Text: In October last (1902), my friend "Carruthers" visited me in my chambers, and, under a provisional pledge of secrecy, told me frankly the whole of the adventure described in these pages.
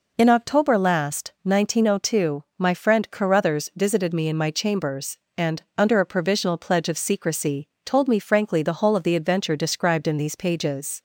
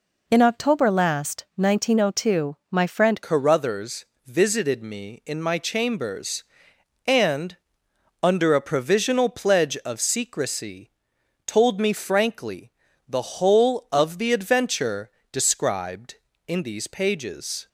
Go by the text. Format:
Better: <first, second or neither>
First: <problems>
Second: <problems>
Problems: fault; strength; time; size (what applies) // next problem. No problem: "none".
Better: first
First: none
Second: changes voice at "Carruthers"; from 3.2 s on; 14.4 s long // pauses between "Carruthers" and "visited"; slight; at 4.0 s; 0.20 s long // pauses between "frankly" and "the"; slight; at 12.7 s; 0.34 s long // pauses between "adventure" and "described"; slight; at 15.0 s; 0.20 s long